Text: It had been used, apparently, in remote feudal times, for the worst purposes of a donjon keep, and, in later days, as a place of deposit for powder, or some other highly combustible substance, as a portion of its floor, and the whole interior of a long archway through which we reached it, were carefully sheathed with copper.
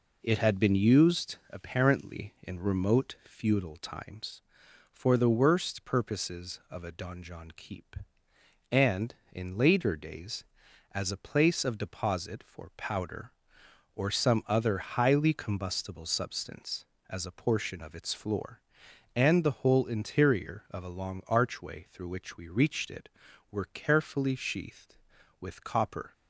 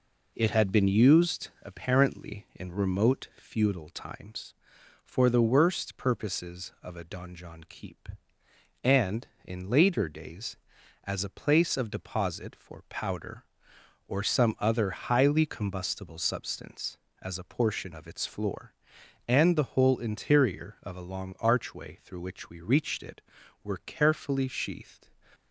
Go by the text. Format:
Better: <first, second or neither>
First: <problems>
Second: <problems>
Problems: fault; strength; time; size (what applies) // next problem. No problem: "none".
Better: first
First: none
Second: stops before "with copper"; at 25.3 s